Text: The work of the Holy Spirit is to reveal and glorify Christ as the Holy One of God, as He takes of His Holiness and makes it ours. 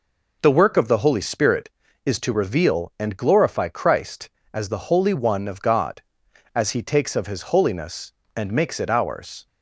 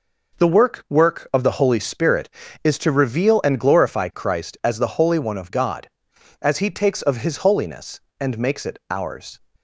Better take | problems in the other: first | says "work" twice; at 0.8 s

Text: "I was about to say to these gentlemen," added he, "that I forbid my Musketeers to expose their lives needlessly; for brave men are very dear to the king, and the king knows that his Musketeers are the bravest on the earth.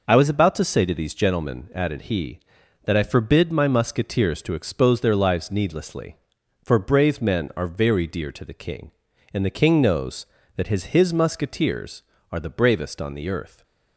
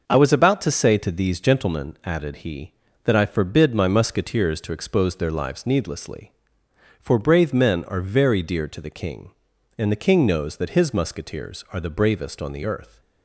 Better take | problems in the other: second | says "his" twice; at 10.8 s

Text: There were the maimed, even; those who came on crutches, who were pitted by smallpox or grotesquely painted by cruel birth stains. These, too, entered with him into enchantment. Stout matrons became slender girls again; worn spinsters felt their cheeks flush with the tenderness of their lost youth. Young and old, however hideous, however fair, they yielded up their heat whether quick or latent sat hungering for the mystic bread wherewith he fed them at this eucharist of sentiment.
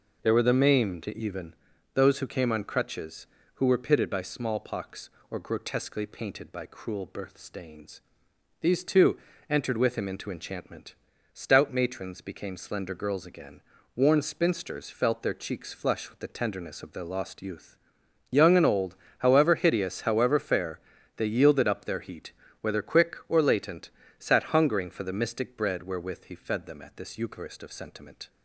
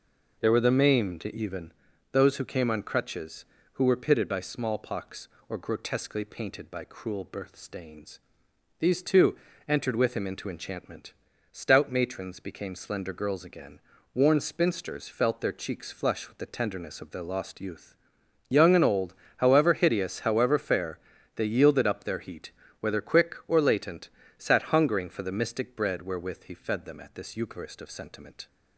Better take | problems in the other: neither | pauses between "heat" and "whether"; slight; the same in both // pauses between "latent" and "sat"; slight; the same in both

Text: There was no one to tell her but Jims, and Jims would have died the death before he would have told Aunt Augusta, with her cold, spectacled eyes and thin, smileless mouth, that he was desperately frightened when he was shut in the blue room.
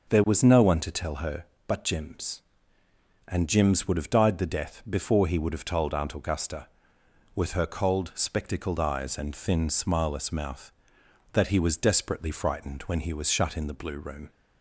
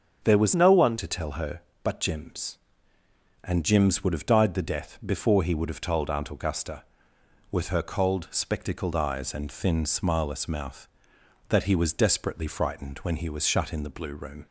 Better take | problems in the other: first | starts louder than the rest; until 1.2 s; 7 dB // changes voice from "no" to "one"; from 0.5 to 0.9 s; 0.4 s long

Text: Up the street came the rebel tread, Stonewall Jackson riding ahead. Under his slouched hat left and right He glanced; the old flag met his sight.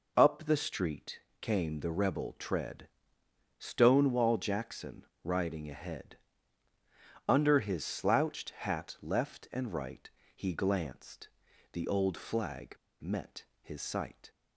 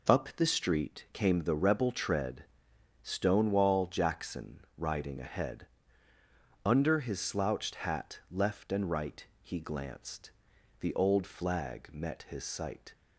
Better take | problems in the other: second | pauses between "street" and "came"; slight; at 1.1 s; 0.22 s long // pauses between "Jackson" and "riding"; slight; at 5.0 s; 0.22 s long; slight in the second // pauses between "right" and "He"; slight; at 10.0 s; 0.24 s long; slight in the second // pauses between "flag" and "met"; slight; at 12.7 s; 0.26 s long // pauses between "met" and "his"; slight; at 13.4 s; 0.16 s long

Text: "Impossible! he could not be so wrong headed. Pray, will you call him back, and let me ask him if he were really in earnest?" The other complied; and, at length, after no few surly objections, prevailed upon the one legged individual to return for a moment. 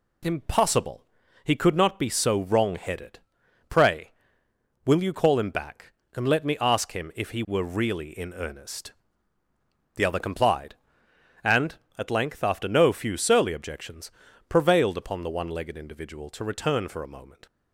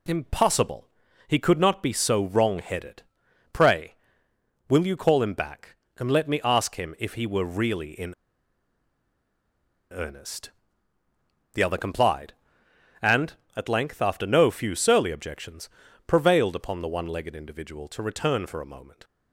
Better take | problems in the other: first | pauses between "in" and "earnest"; strong; at 8.1 s; 1.7 s long

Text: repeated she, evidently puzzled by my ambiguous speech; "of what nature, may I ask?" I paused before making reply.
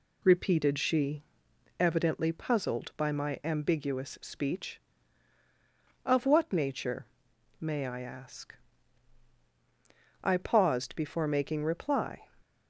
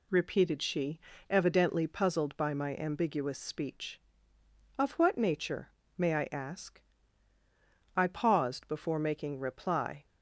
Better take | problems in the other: neither | none

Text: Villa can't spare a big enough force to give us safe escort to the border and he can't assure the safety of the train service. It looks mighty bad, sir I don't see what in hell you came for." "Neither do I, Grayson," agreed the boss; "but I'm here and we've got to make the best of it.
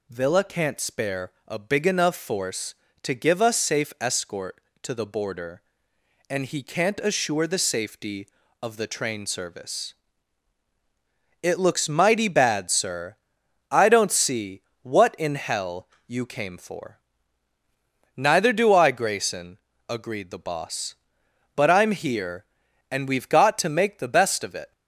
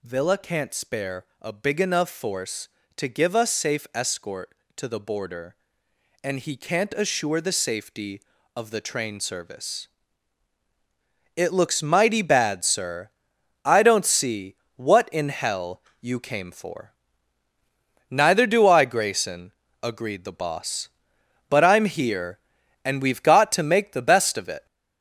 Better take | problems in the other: first | gets louder; noticeable; throughout; 4 dB // pauses between "sir" and "I"; noticeable; at 13.0 s; 0.54 s long; noticeable in the first // pauses between "see" and "what"; slight; at 14.5 s; 0.20 s long; slight in the first // pauses between "hell" and "you"; slight; at 15.8 s; 0.16 s long; slight in the first

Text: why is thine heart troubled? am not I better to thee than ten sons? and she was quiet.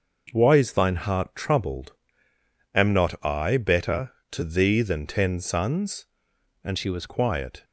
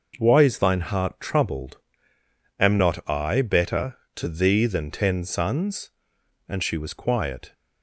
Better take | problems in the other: second | changes voice from "she" to "was"; from 6.7 to 7.0 s; 0.3 s long

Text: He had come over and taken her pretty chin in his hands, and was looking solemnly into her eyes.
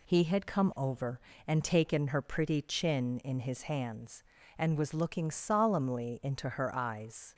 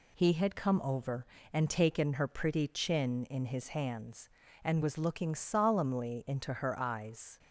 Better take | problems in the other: neither | none

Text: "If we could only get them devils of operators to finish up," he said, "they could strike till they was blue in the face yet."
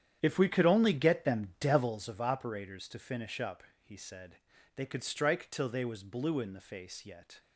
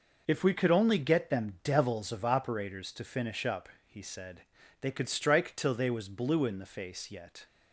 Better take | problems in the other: second | starts louder than the rest; strong; until 2.0 s; 9.5 dB

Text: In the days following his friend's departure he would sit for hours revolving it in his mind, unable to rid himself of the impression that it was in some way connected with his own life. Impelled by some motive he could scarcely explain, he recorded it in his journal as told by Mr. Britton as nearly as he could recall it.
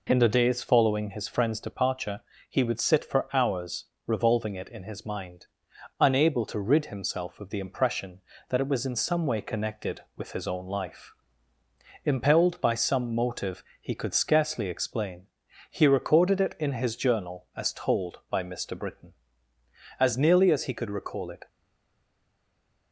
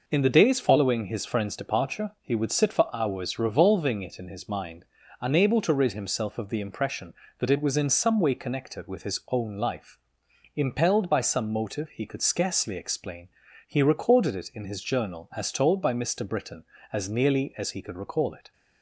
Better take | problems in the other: second | pauses between "departure" and "he"; slight; at 2.2 s; 0.26 s long // pauses between "hours" and "revolving"; slight; at 3.8 s; 0.22 s long // pauses between "motive" and "he"; slight; at 13.6 s; 0.20 s long // stays silent after the last word; noticeable; from 21.4 s on; 1.5 s long

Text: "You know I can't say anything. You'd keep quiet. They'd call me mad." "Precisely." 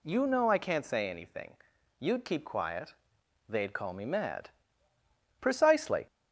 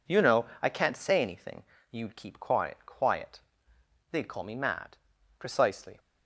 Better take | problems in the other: first | pauses between "know" and "I"; slight; at 0.4 s; 0.18 s long // says "quiet" twice; at 2.8 s

